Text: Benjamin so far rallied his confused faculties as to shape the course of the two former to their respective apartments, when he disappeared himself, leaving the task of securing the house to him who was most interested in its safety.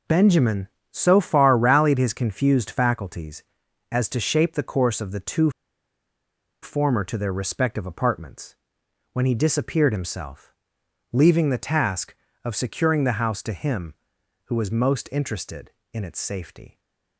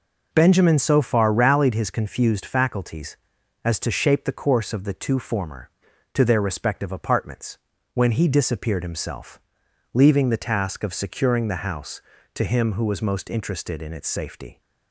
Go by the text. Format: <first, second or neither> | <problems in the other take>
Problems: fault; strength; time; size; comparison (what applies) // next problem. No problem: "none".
second | pauses between "two" and "former"; at 5.4 s; 1.1 s long